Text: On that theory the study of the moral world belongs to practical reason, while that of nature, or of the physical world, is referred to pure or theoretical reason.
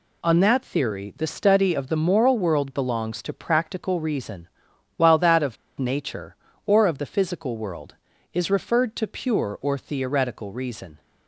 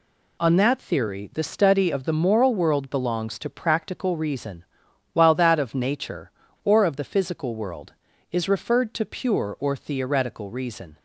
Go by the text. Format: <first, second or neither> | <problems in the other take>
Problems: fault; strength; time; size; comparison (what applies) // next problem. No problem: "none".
second | pauses between "of" and "nature"; slight; at 5.5 s; 0.24 s long